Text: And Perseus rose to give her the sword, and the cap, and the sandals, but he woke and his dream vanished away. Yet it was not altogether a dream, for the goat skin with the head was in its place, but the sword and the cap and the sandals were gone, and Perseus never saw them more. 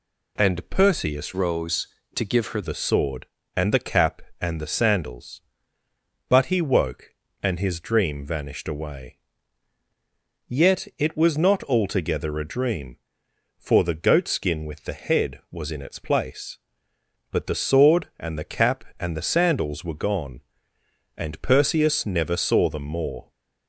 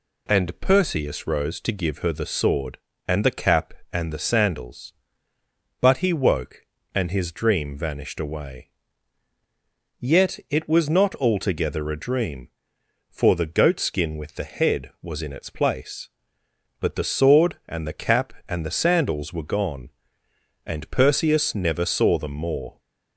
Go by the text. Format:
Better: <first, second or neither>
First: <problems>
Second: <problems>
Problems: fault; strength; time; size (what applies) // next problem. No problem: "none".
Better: second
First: changes voice from "rose" to "her"; from 1.3 to 2.6 s; 1.3 s long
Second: none